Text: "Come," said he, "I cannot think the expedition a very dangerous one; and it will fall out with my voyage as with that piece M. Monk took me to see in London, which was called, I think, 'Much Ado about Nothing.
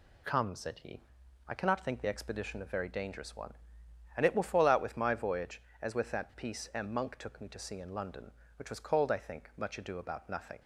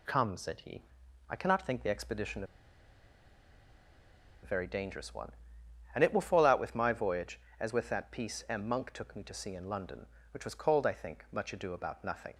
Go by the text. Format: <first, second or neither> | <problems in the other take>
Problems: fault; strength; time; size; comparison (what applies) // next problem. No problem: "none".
first | pauses between "expedition" and "a"; strong; at 2.4 s; 1.9 s long